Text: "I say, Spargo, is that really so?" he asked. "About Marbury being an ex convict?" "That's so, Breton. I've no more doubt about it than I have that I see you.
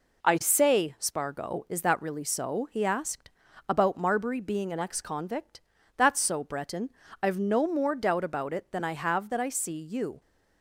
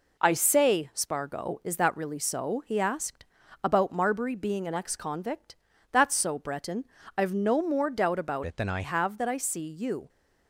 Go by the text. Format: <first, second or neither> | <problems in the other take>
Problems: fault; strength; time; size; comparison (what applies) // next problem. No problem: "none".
first | changes voice from "it" to "I"; from 8.4 to 8.8 s; 0.4 s long